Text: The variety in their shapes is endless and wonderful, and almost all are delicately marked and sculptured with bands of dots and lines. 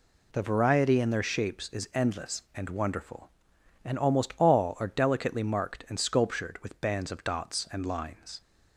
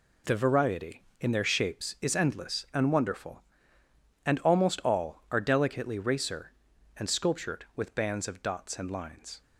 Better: first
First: none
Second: says "racer" for "marked"; at 5.9 s

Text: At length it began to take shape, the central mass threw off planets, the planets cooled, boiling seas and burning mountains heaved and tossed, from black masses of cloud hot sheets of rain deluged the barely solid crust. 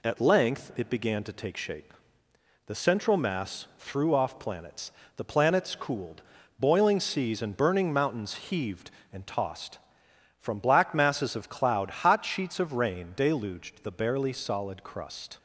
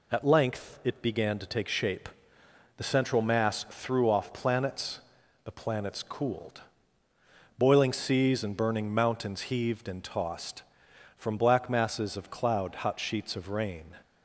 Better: first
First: none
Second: stops before "deluged the barely solid crust"; at 14.0 s

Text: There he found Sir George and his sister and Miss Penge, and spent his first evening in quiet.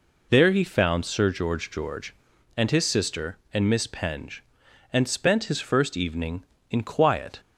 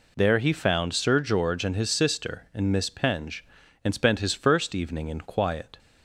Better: second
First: says "George" twice; at 1.7 s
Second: none

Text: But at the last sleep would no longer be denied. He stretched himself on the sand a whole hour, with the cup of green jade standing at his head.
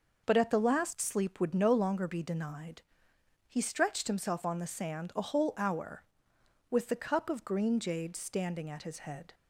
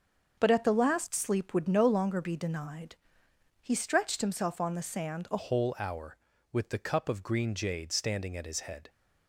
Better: first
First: none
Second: starts louder than the rest; until 1.4 s; 6.5 dB // changes voice at "whole"; from 5.3 s on; 3.5 s long

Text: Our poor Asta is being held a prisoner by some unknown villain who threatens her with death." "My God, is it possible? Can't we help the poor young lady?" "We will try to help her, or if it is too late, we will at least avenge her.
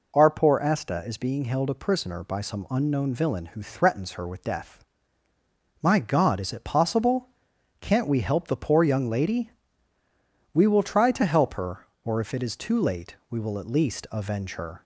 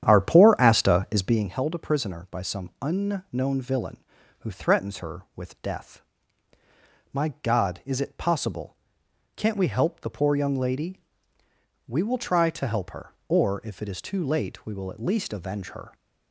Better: first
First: none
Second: starts louder than the rest; strong; until 1.5 s; 9.5 dB

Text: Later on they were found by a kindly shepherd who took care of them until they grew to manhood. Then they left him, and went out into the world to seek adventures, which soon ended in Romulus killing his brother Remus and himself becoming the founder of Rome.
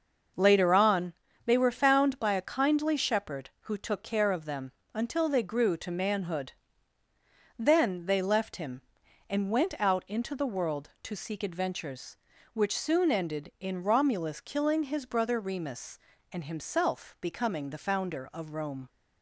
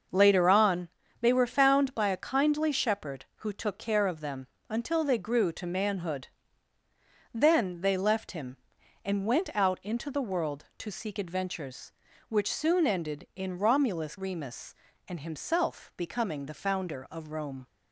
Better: first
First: starts louder than the rest; until 1.6 s; 6 dB // pauses between "on" and "they"; slight; at 1.1 s; 0.32 s long // pauses between "them" and "until"; slight; at 4.7 s; 0.22 s long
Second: starts louder than the rest; until 1.4 s; 6 dB // pauses between "on" and "they"; slight; at 0.8 s; 0.32 s long // pauses between "them" and "until"; slight; at 4.4 s; 0.22 s long // skips "killing his brother"; at 14.1 s

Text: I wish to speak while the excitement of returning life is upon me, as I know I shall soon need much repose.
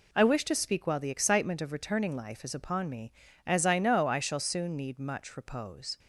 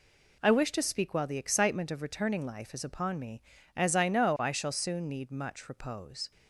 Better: neither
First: none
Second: none

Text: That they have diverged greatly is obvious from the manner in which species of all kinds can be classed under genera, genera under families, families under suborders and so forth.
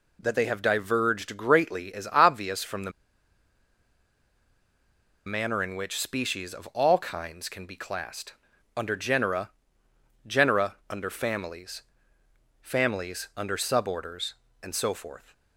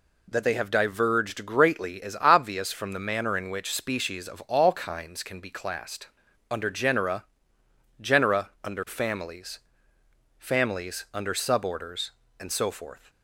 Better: second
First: pauses between "the" and "manner"; strong; at 2.9 s; 2.3 s long // pauses between "classed" and "under"; at 8.3 s; 0.44 s long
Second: pauses between "classed" and "under"; at 6.0 s; 0.44 s long

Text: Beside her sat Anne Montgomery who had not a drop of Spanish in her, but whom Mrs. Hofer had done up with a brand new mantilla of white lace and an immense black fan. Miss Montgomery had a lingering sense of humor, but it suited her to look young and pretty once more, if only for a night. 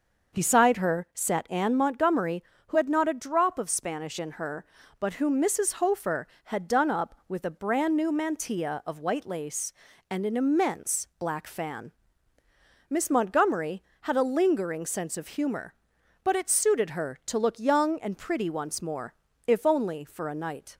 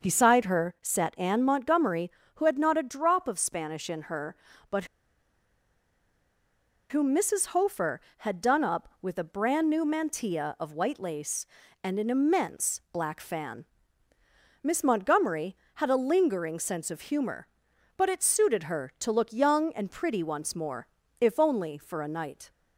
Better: first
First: starts louder than the rest; noticeable; until 1.4 s; 6 dB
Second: starts louder than the rest; noticeable; until 1.1 s; 6 dB // pauses between "but" and "whom"; strong; at 4.8 s; 2.0 s long

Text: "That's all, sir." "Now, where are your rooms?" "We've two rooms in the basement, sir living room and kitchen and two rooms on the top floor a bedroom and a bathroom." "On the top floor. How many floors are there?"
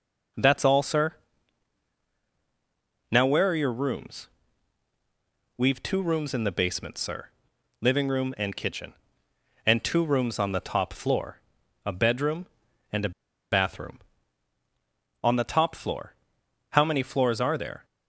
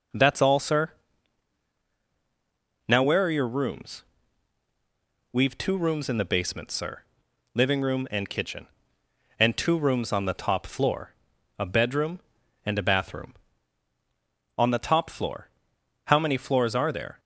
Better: second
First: pauses between "sir" and "living"; noticeable; at 7.2 s; 0.52 s long // pauses between "floor" and "a"; at 11.3 s; 0.44 s long // pauses between "a" and "bathroom"; at 13.0 s; 0.41 s long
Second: pauses between "sir" and "living"; noticeable; at 7.0 s; 0.52 s long // pauses between "floor" and "a"; at 11.1 s; 0.44 s long

